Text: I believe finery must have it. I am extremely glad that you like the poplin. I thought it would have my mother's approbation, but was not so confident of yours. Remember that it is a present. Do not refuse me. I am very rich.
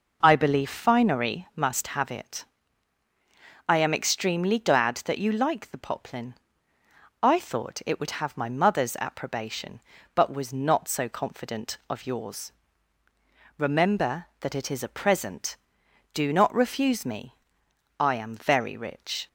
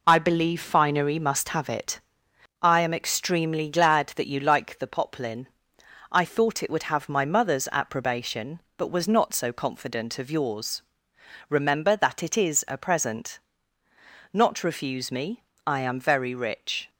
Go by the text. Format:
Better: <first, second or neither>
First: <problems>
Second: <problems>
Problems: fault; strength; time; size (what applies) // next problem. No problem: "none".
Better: first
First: none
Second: skips "Do"; at 13.8 s